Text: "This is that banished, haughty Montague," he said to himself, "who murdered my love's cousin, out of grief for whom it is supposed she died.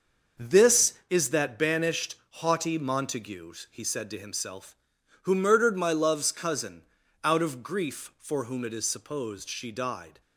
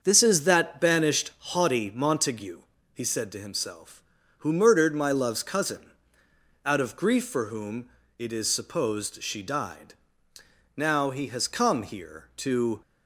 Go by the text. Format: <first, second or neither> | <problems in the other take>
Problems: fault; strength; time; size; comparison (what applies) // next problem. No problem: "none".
first | starts louder than the rest; until 1.0 s; 7 dB; also in the first // pauses between "whom" and "it"; slight; at 7.8 s; 0.30 s long // goes on to say "Now he has come here to"; strong; from 10.7 s on; 2.0 s long